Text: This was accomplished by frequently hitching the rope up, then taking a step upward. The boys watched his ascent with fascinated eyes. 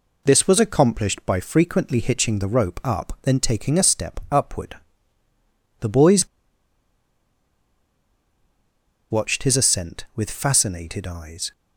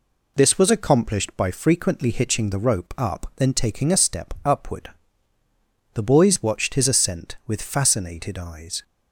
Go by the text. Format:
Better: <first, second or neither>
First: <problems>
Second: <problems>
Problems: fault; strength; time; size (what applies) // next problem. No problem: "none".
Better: second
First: pauses between "boys" and "watched"; strong; at 6.2 s; 2.8 s long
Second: none